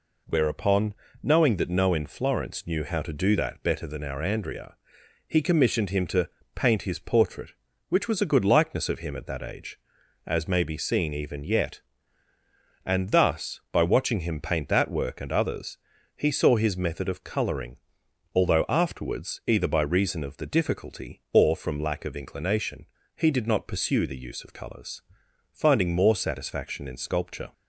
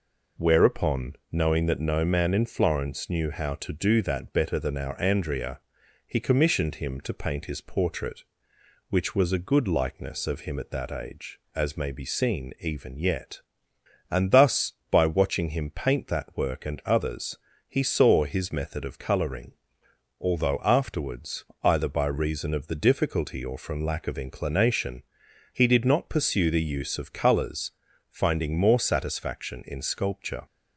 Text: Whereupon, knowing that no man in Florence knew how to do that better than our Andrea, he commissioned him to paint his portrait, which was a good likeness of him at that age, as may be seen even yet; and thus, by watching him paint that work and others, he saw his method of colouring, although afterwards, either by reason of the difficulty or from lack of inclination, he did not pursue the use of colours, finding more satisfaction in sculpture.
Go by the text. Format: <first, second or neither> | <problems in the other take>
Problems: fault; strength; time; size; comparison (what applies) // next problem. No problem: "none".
second | skips "man"; at 1.9 s // pauses between "to" and "paint"; slight; at 6.2 s; 0.26 s long